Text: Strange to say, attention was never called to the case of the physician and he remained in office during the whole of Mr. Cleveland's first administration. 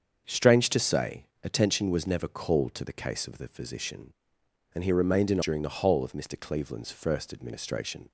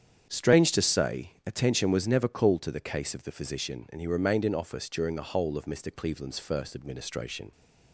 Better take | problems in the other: second | starts louder than the rest; until 1.2 s; 7 dB; strong in the second // skips "office"; at 5.4 s

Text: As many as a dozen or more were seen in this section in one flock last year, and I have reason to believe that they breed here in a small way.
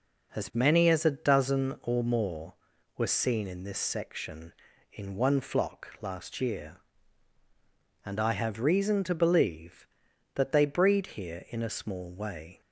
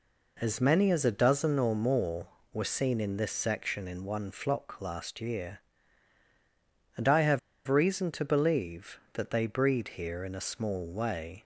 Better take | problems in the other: first | pauses between "have" and "reason"; slight; at 7.3 s; 0.27 s long

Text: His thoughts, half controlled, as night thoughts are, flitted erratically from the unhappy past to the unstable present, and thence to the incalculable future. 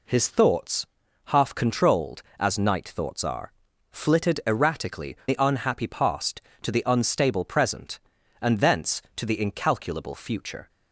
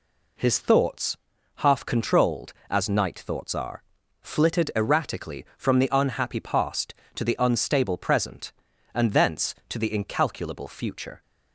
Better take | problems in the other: second | skips "from"; at 5.2 s

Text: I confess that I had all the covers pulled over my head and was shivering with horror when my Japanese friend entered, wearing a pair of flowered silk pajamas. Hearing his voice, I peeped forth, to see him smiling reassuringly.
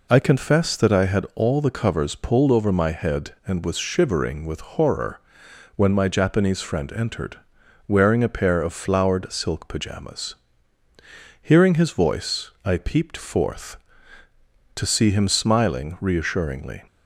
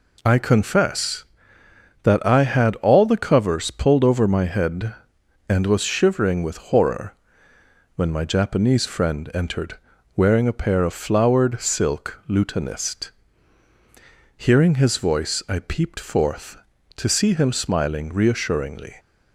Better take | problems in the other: first | pauses between "horror" and "when"; noticeable; at 7.1 s; 0.80 s long; noticeable in the first // says "lutanist" for "pajamas"; at 12.2 s

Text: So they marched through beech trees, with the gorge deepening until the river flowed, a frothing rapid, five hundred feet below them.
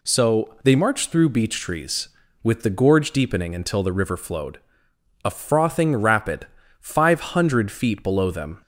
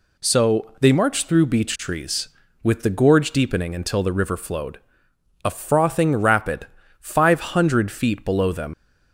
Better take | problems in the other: first | leaves "them" unfinished; at 8.7 s; 85 ms

